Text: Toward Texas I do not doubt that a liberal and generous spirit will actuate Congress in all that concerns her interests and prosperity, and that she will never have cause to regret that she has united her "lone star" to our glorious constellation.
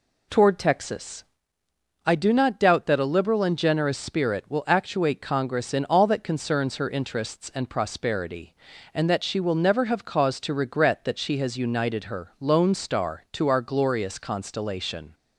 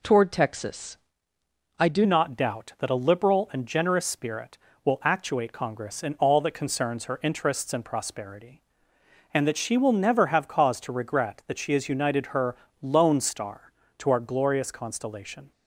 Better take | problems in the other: first | pauses between "Texas" and "I"; noticeable; at 0.9 s; 0.82 s long; noticeable in the first // changes voice at "not"; from 2.0 s on; 13.5 s long // pauses between "her" and "lone"; slight; at 12.5 s; 0.26 s long

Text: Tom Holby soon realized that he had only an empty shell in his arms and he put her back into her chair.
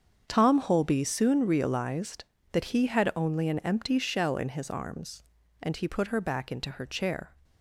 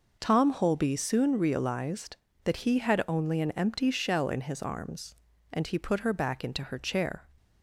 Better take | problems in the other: second | gets quieter; strong; throughout; 13.5 dB

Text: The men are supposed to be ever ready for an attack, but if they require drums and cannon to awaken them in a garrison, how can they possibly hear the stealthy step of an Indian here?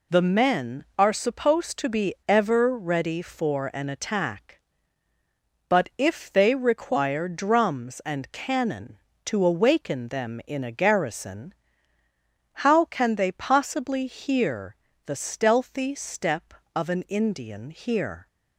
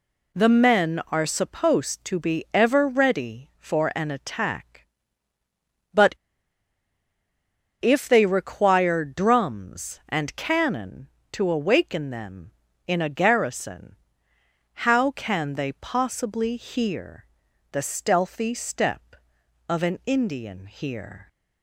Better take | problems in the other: first | pauses between "but" and "if"; strong; at 6.1 s; 1.6 s long // pauses between "hear" and "the"; at 17.2 s; 0.44 s long; slight in the first

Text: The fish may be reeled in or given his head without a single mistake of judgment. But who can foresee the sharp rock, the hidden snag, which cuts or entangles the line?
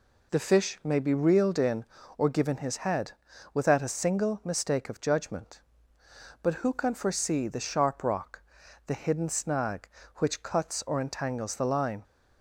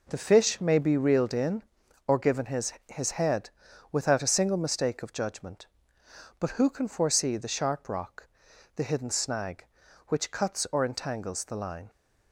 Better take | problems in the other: first | says "his" twice; at 2.8 s // pauses between "head" and "without"; at 3.4 s; 0.42 s long; also in the first

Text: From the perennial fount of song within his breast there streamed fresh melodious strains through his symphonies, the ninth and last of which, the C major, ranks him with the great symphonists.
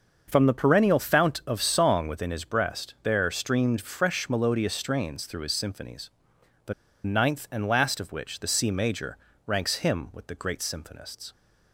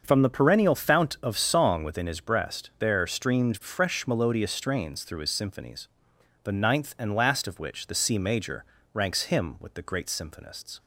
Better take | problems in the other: second | starts louder than the rest; until 1.2 s; 6.5 dB; also in the second // pauses between "the" and "ninth"; slight; at 6.7 s; 0.32 s long

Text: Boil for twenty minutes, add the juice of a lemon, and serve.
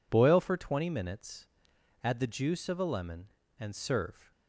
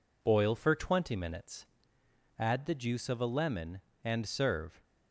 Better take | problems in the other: neither | none

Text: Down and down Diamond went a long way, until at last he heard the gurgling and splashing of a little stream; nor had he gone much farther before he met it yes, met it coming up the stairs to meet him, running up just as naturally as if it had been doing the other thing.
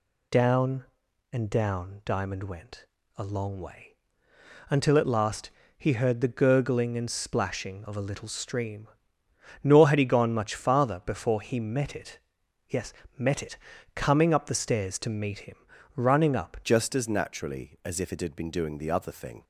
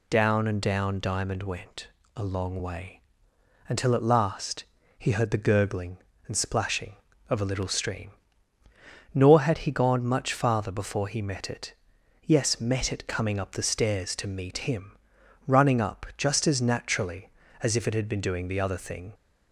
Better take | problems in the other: second | pauses between "went" and "a"; slight; at 2.8 s; 0.30 s long; slight in the second // pauses between "last" and "he"; slight; at 5.5 s; 0.26 s long; slight in the second // pauses between "it" and "yes"; noticeable; at 12.1 s; 0.50 s long; noticeable in the second // pauses between "it" and "coming"; at 13.5 s; 0.38 s long // changes voice at "just"; from 16.6 s on; 2.8 s long

